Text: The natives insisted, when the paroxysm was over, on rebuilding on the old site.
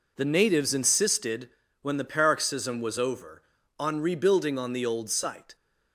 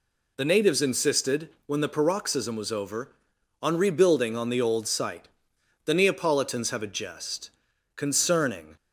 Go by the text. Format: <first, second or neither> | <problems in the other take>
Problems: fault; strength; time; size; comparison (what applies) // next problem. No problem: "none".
first | goes on to say "The Neapolitans have a jest concerning"; strong; from 5.8 s on; 2.9 s long